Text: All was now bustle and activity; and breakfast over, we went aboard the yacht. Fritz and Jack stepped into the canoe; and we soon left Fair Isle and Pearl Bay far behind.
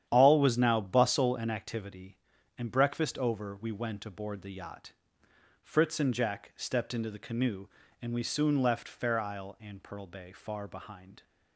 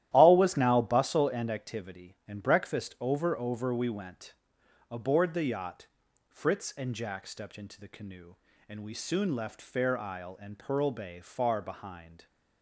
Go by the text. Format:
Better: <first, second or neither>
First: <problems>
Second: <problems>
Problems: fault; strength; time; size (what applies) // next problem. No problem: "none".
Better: first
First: starts louder than the rest; strong; until 1.0 s; 10 dB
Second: starts louder than the rest; strong; until 1.1 s; 13 dB // says "over" twice; at 3.3 s // pauses between "went" and "aboard"; noticeable; at 4.3 s; 0.56 s long